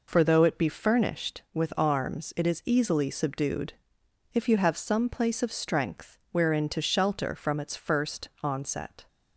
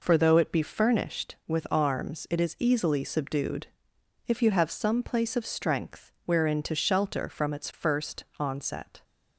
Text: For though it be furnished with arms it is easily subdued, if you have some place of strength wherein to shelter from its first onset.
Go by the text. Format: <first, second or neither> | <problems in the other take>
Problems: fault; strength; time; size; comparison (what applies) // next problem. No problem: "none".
neither | none